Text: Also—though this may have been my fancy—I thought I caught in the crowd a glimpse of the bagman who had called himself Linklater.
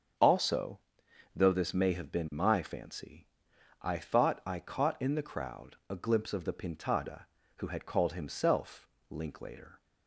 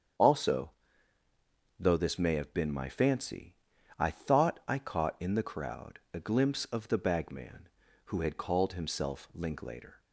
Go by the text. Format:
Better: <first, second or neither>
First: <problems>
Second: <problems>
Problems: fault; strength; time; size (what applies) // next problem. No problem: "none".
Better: second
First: starts louder than the rest; strong; until 1.7 s; 7 dB // says "pintada" for "bagman"; at 6.5 s // pauses between "himself" and "Linklater"; slight; at 8.8 s; 0.24 s long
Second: starts louder than the rest; strong; until 2.2 s; 8 dB